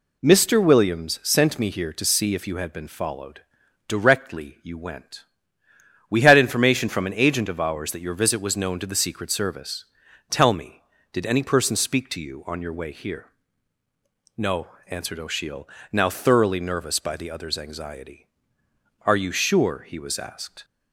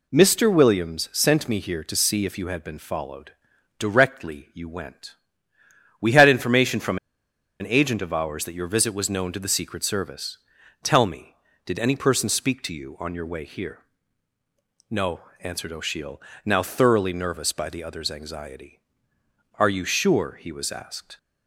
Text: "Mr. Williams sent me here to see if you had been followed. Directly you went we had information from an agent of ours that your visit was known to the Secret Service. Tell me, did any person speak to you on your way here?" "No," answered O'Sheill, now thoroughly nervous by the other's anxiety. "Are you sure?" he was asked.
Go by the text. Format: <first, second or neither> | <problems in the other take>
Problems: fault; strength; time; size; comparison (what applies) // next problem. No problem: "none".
first | pauses between "went" and "we"; noticeable; at 5.1 s; 0.86 s long; noticeable in the first // pauses between "from" and "an"; noticeable; at 6.9 s; 0.63 s long